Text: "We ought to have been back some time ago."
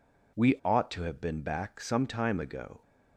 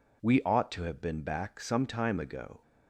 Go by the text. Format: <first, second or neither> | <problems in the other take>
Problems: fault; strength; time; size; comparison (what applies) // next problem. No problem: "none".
neither | none